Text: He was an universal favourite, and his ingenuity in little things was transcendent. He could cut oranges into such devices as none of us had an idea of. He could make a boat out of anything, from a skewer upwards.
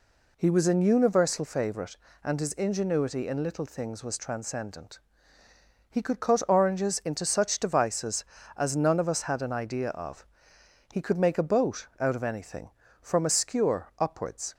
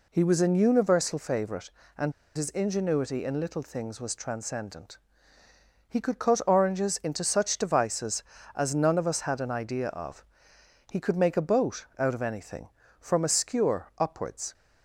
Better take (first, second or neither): first